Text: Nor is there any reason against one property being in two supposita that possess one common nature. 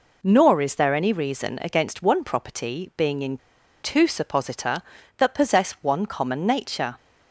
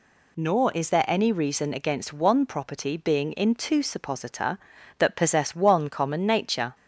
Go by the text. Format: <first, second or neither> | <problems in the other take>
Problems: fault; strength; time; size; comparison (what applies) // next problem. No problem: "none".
second | pauses between "in" and "two"; at 3.3 s; 0.44 s long